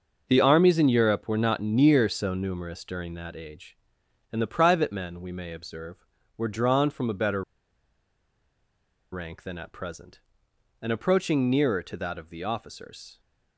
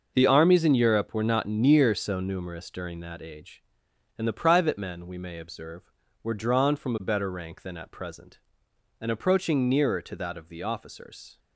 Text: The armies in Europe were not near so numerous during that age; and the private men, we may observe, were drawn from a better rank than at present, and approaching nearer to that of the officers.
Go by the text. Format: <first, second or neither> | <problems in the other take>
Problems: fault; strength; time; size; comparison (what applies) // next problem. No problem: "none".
second | starts louder than the rest; until 1.3 s; 6 dB; also in the second // pauses between "better" and "rank"; strong; at 7.4 s; 1.7 s long